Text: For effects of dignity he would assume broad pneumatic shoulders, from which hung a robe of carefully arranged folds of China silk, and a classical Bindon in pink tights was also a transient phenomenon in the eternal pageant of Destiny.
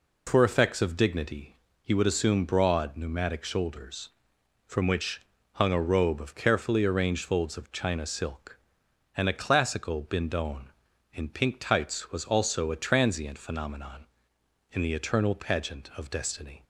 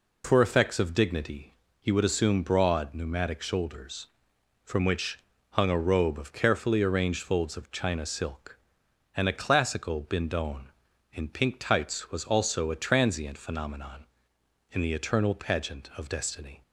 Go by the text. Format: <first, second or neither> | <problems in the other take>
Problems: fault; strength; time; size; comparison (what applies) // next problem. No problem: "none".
neither | pauses between "dignity" and "he"; slight; the same in both // pauses between "which" and "hung"; slight; the same in both